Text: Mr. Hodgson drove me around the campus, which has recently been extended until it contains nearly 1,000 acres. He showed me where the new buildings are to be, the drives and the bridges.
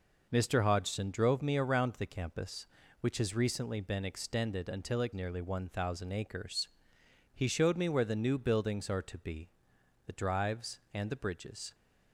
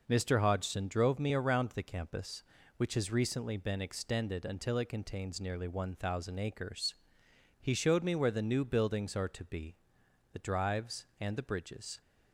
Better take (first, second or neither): second